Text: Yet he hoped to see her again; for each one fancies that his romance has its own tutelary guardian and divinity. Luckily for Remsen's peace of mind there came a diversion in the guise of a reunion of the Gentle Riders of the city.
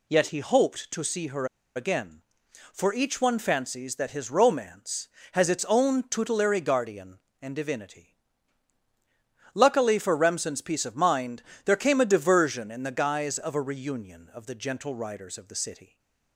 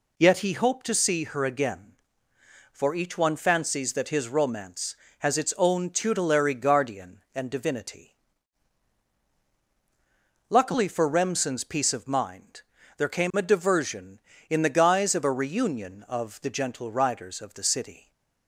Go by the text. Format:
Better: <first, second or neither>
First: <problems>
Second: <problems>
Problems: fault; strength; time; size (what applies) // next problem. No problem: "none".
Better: second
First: pauses between "her" and "again"; slight; at 1.4 s; 0.29 s long // pauses between "mind" and "there"; slight; at 11.4 s; 0.24 s long // stays silent after the last word; slight; from 15.8 s on; 0.5 s long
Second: pauses between "mind" and "there"; slight; at 12.6 s; 0.34 s long